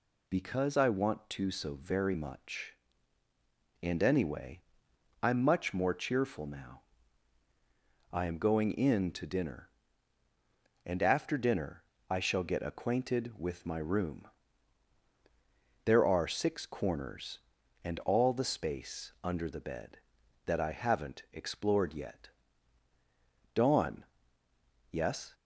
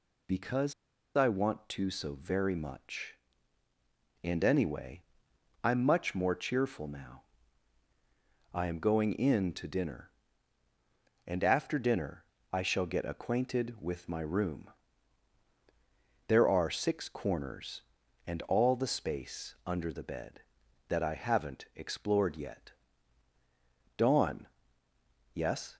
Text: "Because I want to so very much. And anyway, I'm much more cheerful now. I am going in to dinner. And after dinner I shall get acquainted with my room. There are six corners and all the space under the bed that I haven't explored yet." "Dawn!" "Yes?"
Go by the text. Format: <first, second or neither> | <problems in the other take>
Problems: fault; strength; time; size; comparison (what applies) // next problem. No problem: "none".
first | pauses between "Because" and "I"; at 0.7 s; 0.42 s long // pauses between "dinner" and "I"; slight; at 12.2 s; 0.28 s long; slight in the first